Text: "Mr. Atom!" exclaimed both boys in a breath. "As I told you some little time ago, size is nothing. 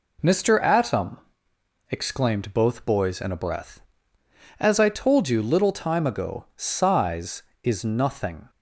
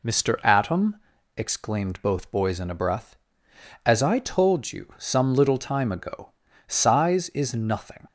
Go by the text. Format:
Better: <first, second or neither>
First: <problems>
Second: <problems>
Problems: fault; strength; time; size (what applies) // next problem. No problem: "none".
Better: second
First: skips "some"; at 5.4 s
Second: none